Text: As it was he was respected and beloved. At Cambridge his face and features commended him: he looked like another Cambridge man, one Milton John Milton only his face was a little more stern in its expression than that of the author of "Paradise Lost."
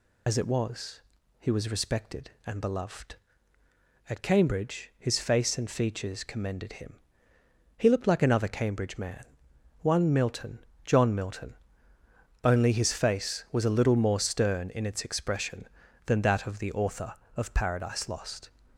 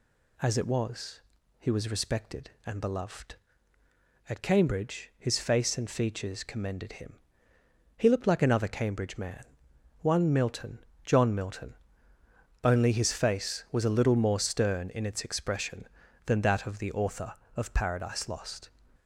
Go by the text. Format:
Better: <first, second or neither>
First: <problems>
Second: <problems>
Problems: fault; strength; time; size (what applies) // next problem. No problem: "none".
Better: second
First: loses the start of "As"; at 0.2 s; 70 ms // pauses between "was" and "he"; at 1.0 s; 0.38 s long // pauses between "Milton" and "John"; slight; at 10.5 s; 0.26 s long // pauses between "Milton" and "only"; noticeable; at 11.5 s; 0.90 s long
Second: pauses between "was" and "he"; at 1.2 s; 0.38 s long // pauses between "Milton" and "John"; slight; at 10.7 s; 0.26 s long // pauses between "Milton" and "only"; noticeable; at 11.7 s; 0.90 s long